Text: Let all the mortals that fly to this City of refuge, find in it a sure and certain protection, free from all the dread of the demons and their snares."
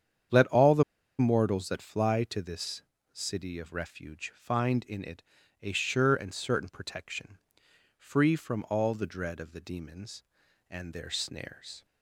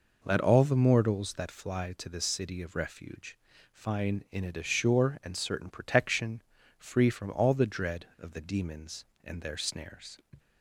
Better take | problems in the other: second | starts louder than the rest; strong; until 1.7 s; 8.5 dB // pauses between "the" and "mortals"; slight; at 0.8 s; 0.36 s long // pauses between "this" and "City"; slight; at 2.8 s; 0.36 s long // pauses between "it" and "a"; at 5.2 s; 0.38 s long

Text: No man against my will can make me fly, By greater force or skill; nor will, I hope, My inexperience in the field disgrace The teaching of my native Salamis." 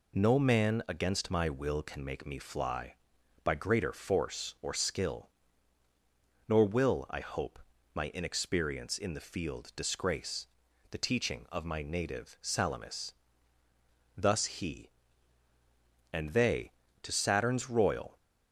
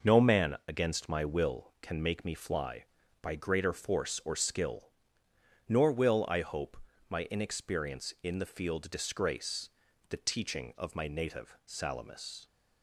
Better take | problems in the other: second | pauses between "disgrace" and "The"; at 10.4 s; 0.44 s long; also in the second // goes on to say "Thus he and they to Saturn's royal"; strong; from 14.1 s on; 4.0 s long

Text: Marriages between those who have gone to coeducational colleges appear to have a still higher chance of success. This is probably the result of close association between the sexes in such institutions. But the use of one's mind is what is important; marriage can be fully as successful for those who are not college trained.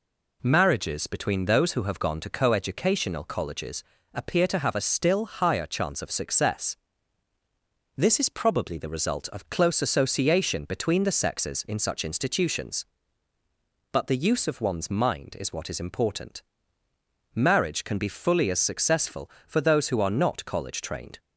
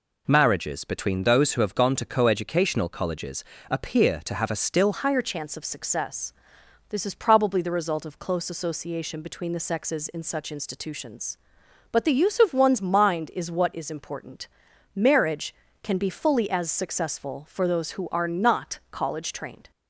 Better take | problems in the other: first | pauses between "colleges" and "appear"; slight; at 3.4 s; 0.26 s long; slight in the first // changes voice at "higher"; from 4.9 s on; 14.8 s long

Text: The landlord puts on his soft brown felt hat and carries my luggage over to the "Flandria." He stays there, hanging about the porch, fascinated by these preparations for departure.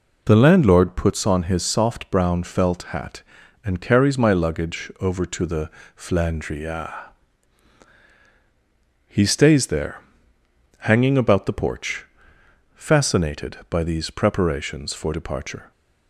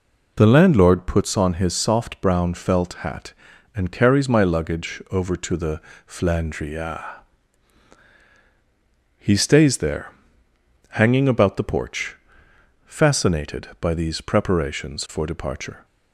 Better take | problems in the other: neither | pauses between "the" and "Flandria"; slight; the same in both

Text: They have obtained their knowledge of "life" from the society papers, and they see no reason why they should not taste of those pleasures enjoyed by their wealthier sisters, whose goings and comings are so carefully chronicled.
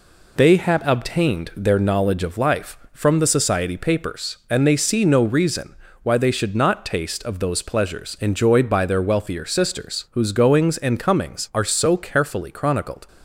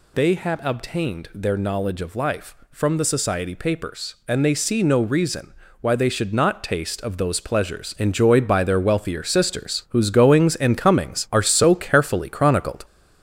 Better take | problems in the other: first | gets louder; noticeable; throughout; 5 dB // pauses between "reason" and "why"; slight; at 5.5 s; 0.28 s long; slight in the first

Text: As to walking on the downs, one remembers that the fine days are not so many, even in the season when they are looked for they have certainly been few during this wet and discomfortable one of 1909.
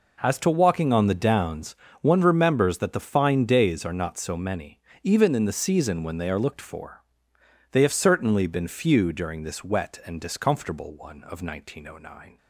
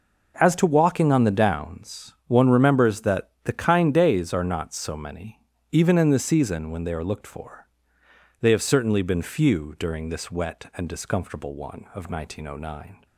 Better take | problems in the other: first | pauses between "that" and "the"; slight; at 3.2 s; 0.16 s long // says "kind" for "fine"; at 3.5 s // pauses between "for" and "they"; noticeable; at 7.6 s; 0.78 s long; noticeable in the first

